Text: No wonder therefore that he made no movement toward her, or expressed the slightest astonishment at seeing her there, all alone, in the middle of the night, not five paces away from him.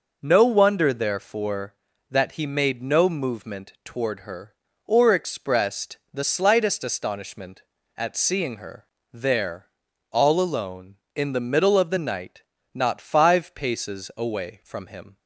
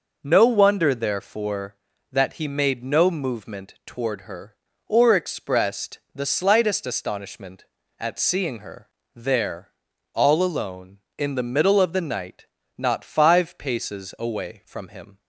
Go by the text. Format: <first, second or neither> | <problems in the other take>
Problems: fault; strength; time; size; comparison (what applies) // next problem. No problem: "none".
neither | pauses between "her" and "there"; slight; the same in both